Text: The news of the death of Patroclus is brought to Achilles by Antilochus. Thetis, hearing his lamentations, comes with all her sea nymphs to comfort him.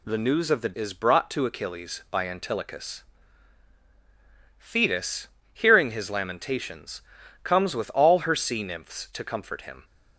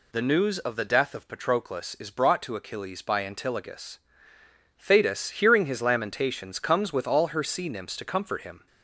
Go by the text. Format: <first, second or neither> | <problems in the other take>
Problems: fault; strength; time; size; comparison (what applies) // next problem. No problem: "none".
second | skips "death of Patroclus"; at 0.7 s